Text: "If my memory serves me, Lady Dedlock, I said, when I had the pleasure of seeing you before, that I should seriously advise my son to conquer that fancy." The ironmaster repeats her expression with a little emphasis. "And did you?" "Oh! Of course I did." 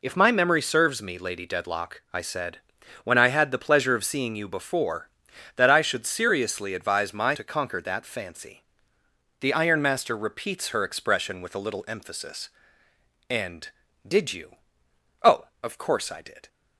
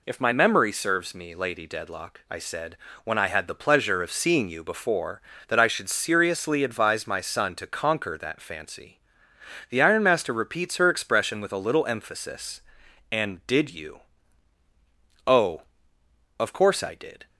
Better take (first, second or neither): second